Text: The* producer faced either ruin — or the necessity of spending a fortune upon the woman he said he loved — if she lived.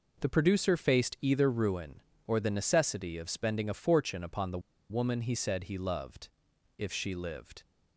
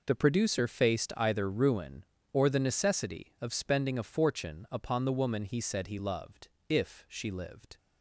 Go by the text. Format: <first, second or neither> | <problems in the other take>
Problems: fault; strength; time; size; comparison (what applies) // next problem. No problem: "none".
second | pauses between "the" and "woman"; slight; at 4.5 s; 0.31 s long